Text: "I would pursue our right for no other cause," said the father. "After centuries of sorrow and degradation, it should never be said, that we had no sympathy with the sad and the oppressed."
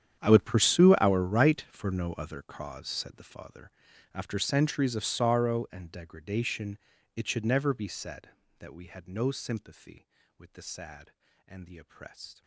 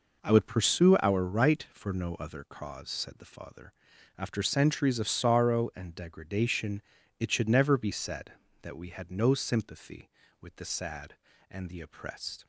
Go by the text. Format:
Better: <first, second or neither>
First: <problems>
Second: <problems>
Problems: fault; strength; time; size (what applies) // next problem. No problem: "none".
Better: second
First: gets quieter; strong; throughout; 18 dB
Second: none